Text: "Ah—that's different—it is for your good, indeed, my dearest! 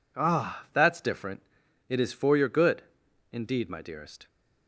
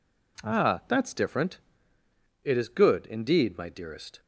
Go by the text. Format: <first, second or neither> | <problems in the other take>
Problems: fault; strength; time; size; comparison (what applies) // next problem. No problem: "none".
first | skips "for your"; at 2.6 s